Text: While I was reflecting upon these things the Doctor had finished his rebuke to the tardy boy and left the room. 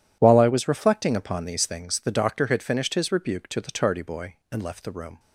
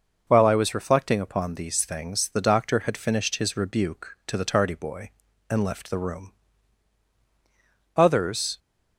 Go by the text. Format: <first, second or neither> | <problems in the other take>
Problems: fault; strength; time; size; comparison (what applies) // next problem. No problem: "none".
first | goes on to say "Others"; noticeable; from 7.9 s on; 0.62 s long